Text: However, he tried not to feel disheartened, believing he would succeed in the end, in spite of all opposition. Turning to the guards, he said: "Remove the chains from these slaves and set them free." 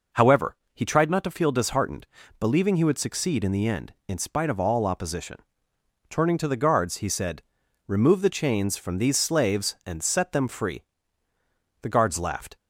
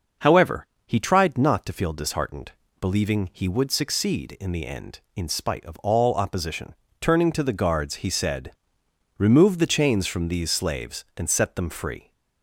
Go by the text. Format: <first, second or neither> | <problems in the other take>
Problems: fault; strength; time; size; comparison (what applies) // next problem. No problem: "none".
second | goes on to say "The guards laughed"; noticeable; from 11.8 s on; 0.74 s long